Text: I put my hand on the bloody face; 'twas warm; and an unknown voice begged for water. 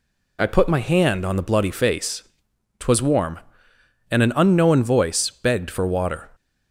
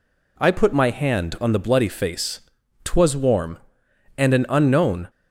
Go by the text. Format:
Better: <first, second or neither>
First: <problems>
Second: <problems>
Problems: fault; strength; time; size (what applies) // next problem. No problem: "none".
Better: first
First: none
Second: stops before "voice begged for water"; at 5.0 s